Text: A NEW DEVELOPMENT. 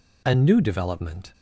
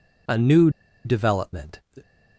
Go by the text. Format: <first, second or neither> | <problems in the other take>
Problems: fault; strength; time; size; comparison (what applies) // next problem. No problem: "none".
first | pauses between "NEW" and "DEVELOPMENT"; slight; at 0.6 s; 0.35 s long